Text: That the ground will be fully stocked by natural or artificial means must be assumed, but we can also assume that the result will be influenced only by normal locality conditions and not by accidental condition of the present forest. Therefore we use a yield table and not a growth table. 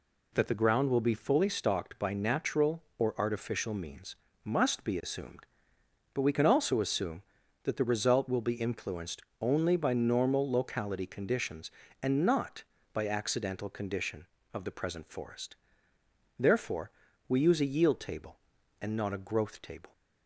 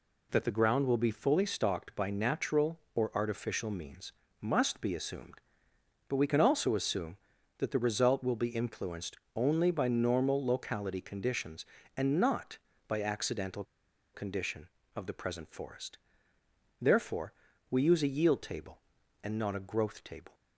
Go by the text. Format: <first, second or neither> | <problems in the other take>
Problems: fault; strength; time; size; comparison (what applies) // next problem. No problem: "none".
first | pauses between "means" and "must"; slight; at 4.1 s; 0.28 s long; slight in the first // pauses between "influenced" and "only"; slight; at 9.1 s; 0.18 s long; slight in the first // pauses between "accidental" and "condition"; noticeable; at 13.6 s; 0.49 s long // pauses between "Therefore" and "we"; at 17.3 s; 0.40 s long; also in the first